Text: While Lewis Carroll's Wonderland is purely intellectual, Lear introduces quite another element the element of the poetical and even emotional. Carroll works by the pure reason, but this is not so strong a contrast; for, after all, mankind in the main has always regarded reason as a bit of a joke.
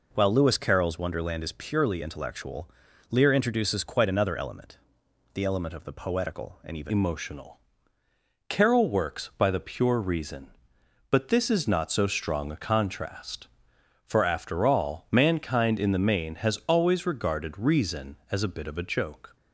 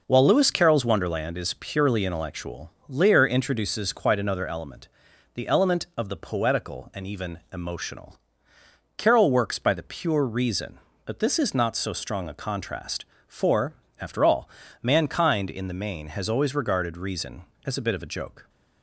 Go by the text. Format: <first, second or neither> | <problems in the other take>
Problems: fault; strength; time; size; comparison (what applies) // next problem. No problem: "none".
second | pauses between "element" and "the"; noticeable; at 4.7 s; 0.56 s long; also in the second // changes voice at "emotional"; from 6.8 s on; 12.5 s long